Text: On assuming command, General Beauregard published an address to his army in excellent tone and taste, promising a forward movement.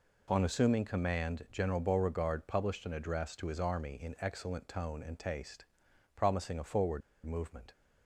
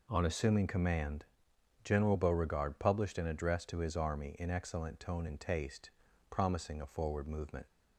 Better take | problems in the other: second | pauses between "forward" and "movement"; slight; at 7.0 s; 0.24 s long

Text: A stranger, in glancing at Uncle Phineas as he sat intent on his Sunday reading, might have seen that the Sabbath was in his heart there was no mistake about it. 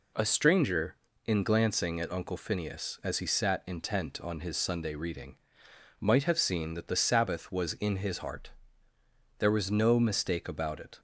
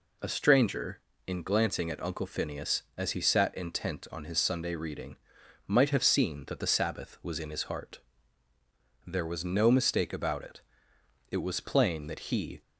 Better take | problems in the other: first | pauses between "heart" and "there"; at 8.0 s; 1.0 s long; noticeable in the first // goes on to say "It was plain that he"; noticeable; from 11.3 s on; 1.3 s long

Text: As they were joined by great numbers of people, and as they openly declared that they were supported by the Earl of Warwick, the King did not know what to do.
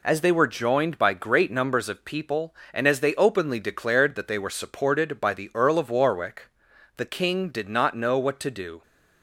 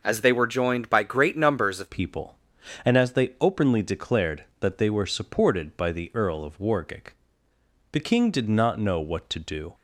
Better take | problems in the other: first | changes voice at "people"; from 1.8 s on; 7.9 s long

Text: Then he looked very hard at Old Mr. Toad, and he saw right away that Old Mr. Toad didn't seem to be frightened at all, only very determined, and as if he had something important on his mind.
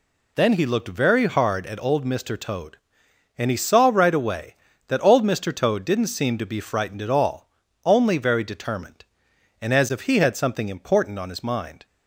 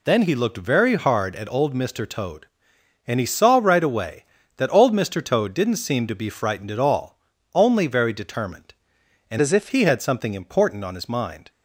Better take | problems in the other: first | changes voice from "as" to "if"; from 9.4 to 9.6 s; 0.2 s long

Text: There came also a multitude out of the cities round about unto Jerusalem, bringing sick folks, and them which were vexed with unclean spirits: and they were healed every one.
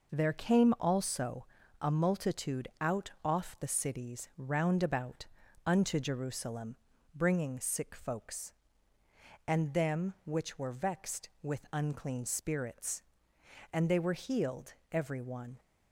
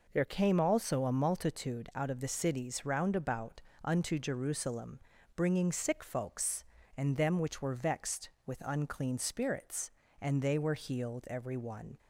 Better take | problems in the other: second | pauses between "also" and "a"; slight; at 1.4 s; 0.34 s long // says "off" for "of"; at 3.2 s // pauses between "about" and "unto"; at 5.2 s; 0.42 s long; slight in the second // pauses between "healed" and "every"; slight; at 14.7 s; 0.18 s long

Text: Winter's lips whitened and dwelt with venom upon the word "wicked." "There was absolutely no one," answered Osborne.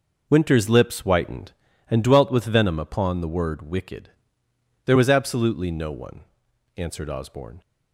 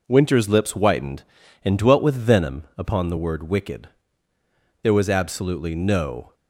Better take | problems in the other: first | stops before "one answered Osborne"; at 6.3 s

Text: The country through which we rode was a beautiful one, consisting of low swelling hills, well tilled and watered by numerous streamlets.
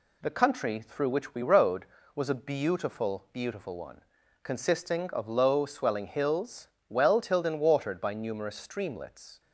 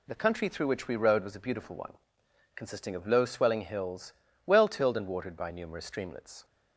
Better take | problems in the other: second | says "beautiful" twice; at 3.3 s

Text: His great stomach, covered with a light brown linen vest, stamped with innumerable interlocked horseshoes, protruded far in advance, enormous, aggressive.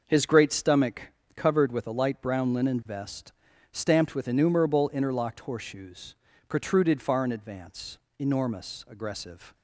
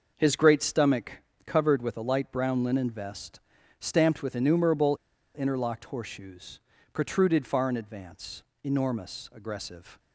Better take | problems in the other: first | pauses between "innumerable" and "interlocked"; at 4.9 s; 0.39 s long

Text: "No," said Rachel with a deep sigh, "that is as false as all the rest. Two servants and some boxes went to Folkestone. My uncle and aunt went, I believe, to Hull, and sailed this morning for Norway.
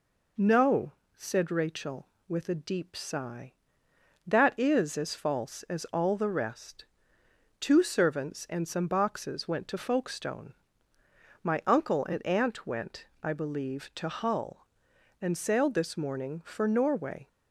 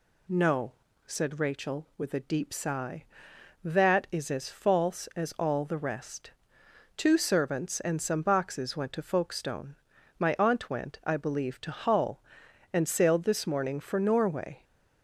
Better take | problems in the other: first | skips "uncle and"; at 10.3 s

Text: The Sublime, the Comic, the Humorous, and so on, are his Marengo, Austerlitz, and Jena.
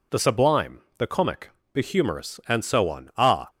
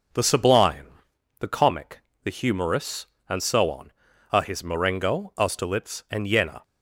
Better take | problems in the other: second | stops before "his Marengo Austerlitz and Jena"; at 3.4 s

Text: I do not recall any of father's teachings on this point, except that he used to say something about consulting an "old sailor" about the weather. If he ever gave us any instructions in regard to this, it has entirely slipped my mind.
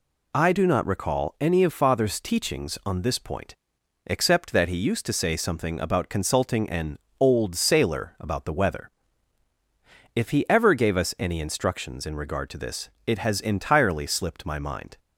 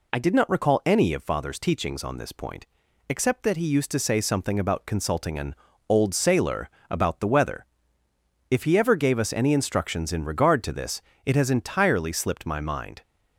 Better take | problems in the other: first | says "did" for "do"; at 0.1 s // pauses between "an" and "old"; slight; at 5.5 s; 0.32 s long; slight in the first // pauses between "sailor" and "about"; slight; at 6.6 s; 0.22 s long

